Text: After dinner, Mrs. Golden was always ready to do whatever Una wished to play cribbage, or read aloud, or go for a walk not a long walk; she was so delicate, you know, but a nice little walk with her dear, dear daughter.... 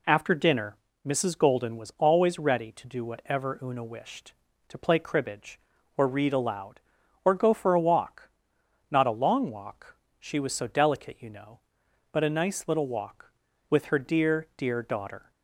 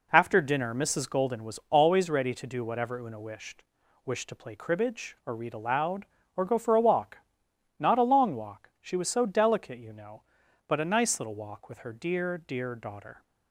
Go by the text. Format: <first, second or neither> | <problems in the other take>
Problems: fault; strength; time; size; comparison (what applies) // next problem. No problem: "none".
first | says "wished" twice; at 4.0 s // pauses between "walk" and "not"; noticeable; at 7.1 s; 0.60 s long; noticeable in the first